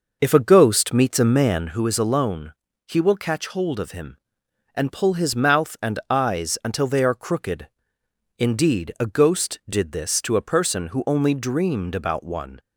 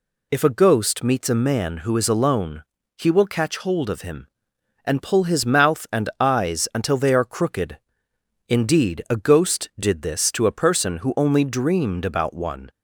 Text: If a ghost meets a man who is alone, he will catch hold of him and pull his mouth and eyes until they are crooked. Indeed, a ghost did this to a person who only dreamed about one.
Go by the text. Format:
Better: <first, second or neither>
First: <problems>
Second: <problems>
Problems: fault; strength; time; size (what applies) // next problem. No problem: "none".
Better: second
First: starts louder than the rest; noticeable; until 1.9 s; 5.5 dB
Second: none